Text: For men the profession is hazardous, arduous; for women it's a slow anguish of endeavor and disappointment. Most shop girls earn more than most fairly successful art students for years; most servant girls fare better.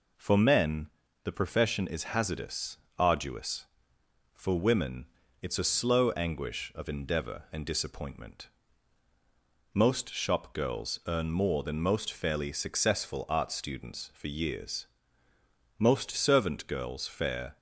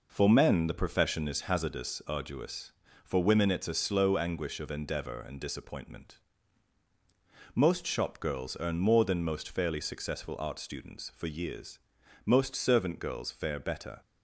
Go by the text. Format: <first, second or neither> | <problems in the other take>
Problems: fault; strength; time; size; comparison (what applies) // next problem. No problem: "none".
second | pauses between "men" and "the"; slight; at 0.8 s; 0.34 s long // pauses between "women" and "it's"; slight; at 5.0 s; 0.34 s long // stops before "better"; at 17.5 s